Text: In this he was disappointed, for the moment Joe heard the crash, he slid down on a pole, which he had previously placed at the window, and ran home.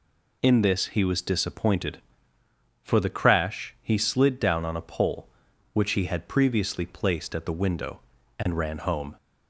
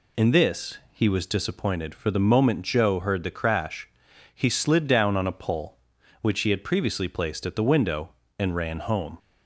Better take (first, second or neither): second